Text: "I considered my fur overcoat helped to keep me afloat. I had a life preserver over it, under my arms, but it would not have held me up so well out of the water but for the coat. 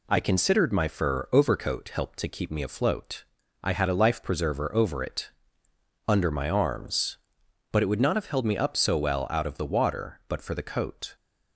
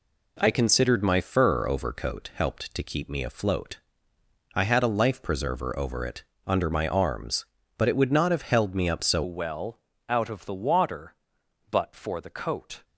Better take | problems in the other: first | changes voice at "well"; from 9.2 s on; 3.6 s long // pauses between "well" and "out"; slight; at 9.7 s; 0.30 s long

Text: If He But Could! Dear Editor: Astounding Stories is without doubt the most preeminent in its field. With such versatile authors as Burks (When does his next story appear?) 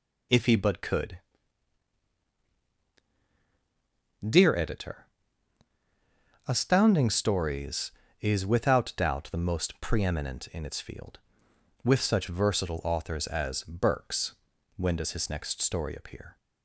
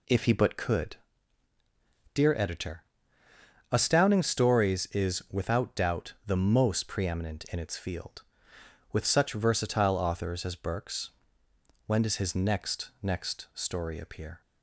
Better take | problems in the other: first | says "next" twice; at 13.0 s

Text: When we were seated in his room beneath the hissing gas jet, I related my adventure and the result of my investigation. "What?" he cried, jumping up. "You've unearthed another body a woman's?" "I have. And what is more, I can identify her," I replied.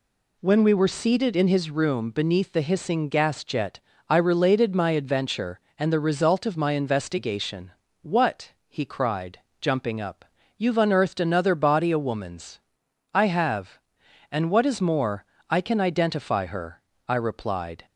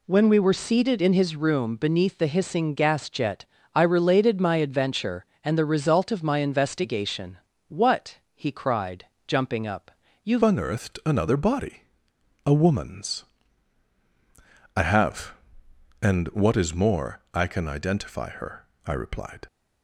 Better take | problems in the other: first | changes voice at "unearthed"; from 10.4 s on; 9.0 s long // pauses between "body" and "a"; noticeable; at 11.8 s; 0.64 s long

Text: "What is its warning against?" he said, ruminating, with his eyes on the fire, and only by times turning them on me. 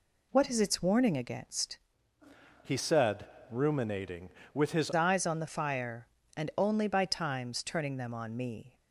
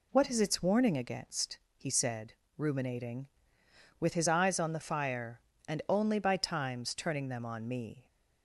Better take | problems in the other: second | changes voice from "he" to "his"; from 2.6 to 4.9 s; 2.3 s long

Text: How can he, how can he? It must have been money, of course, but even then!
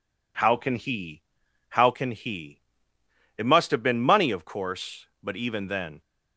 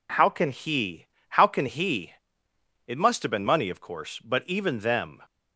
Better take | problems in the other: first | says "them" for "then"; at 4.7 s

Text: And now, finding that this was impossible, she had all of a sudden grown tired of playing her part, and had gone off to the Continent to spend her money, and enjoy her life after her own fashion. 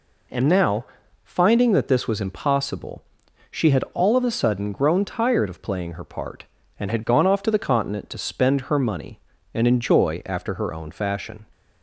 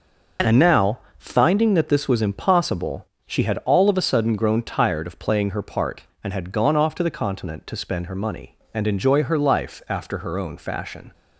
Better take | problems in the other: second | skips "her life"; at 10.2 s

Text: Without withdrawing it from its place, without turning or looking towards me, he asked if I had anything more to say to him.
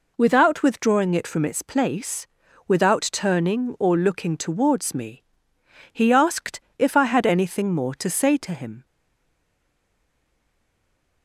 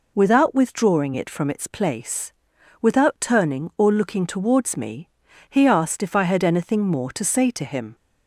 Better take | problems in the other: second | pauses between "asked" and "if"; slight; at 6.6 s; 0.16 s long // stays silent after the last word; from 8.8 s on; 2.4 s long

